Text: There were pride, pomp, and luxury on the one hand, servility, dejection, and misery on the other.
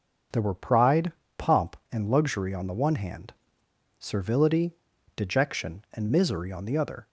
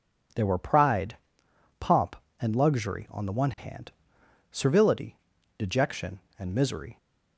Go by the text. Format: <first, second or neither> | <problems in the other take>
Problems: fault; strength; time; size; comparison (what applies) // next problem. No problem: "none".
first | stops before "on the other"; at 6.9 s